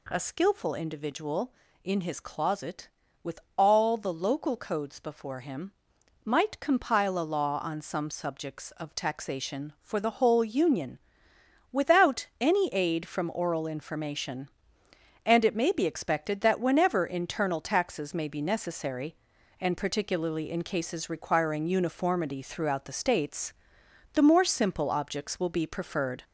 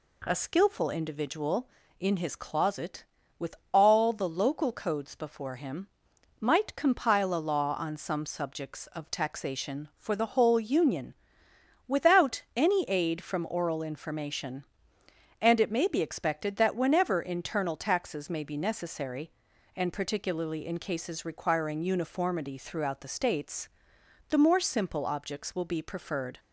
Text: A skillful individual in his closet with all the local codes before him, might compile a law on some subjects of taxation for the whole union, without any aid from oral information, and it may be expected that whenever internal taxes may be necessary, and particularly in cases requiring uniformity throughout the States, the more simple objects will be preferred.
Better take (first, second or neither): second